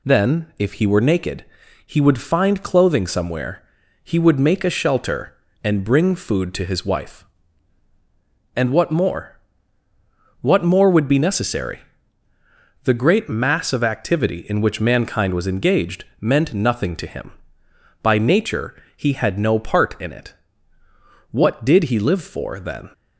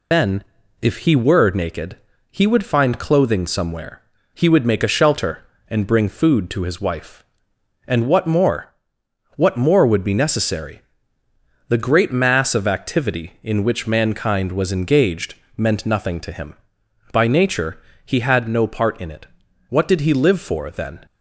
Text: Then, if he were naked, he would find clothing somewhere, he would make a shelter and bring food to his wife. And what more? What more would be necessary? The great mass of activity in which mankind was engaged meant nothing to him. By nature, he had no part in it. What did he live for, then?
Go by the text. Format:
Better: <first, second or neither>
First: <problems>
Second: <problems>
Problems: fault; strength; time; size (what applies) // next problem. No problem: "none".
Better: first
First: none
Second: loses the start of "Then"; at 0.1 s; 135 ms // pauses between "engaged" and "meant"; slight; at 15.3 s; 0.20 s long